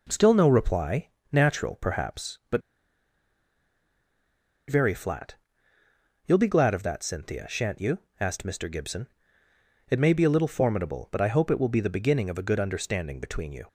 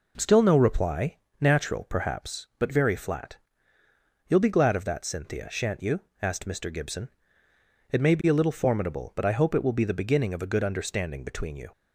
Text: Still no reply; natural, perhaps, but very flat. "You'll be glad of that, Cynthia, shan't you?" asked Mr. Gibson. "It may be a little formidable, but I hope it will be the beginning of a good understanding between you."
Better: second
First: pauses between "but" and "very"; strong; at 2.6 s; 2.0 s long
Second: none

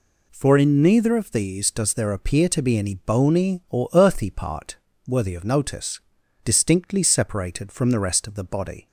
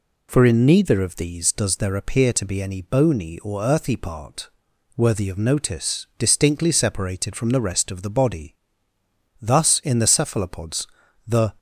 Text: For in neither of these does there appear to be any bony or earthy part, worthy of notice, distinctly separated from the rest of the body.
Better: first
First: none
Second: goes on to say "Thus in the Cephalopods the"; strong; from 9.4 s on; 2.1 s long

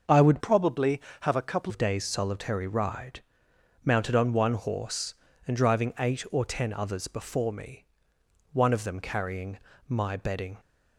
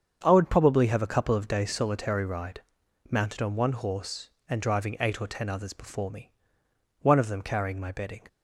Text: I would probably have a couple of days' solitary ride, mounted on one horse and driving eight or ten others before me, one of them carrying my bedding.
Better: second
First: starts louder than the rest; until 1.3 s; 6.5 dB // changes voice from "probably" to "couple"; from 0.3 to 1.7 s; 1.4 s long // pauses between "carrying" and "my"; slight; at 9.5 s; 0.28 s long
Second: starts louder than the rest; strong; until 1.2 s; 7.5 dB

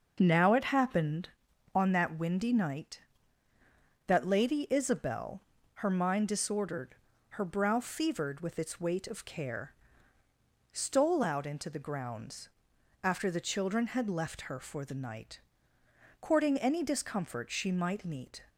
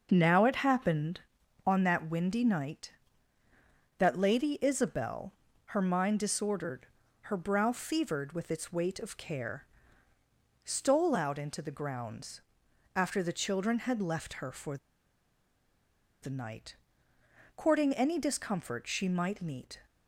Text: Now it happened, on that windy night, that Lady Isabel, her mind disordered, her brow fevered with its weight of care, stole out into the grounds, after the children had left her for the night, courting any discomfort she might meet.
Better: first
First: starts louder than the rest; noticeable; until 1.2 s; 6 dB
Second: starts louder than the rest; noticeable; until 1.1 s; 6 dB // pauses between "for" and "the"; strong; at 14.7 s; 1.4 s long

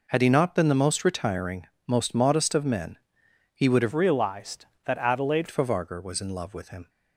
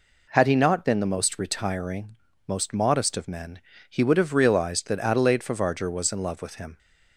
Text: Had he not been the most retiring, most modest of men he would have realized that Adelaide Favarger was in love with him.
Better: second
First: pauses between "men" and "he"; noticeable; at 2.9 s; 0.58 s long // changes voice from "realized" to "Adelaide"; from 3.9 to 5.4 s; 1.5 s long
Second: pauses between "men" and "he"; slight; at 3.5 s; 0.28 s long

